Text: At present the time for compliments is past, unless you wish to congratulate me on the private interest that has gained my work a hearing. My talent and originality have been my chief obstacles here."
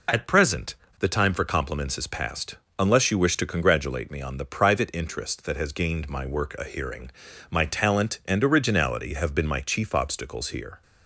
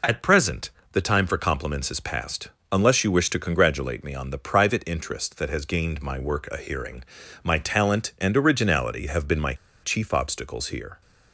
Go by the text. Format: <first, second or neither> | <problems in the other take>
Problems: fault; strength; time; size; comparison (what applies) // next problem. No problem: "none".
first | pauses between "present" and "the"; slight; at 0.6 s; 0.24 s long; slight in the first // pauses between "my" and "chief"; slight; at 9.5 s; 0.28 s long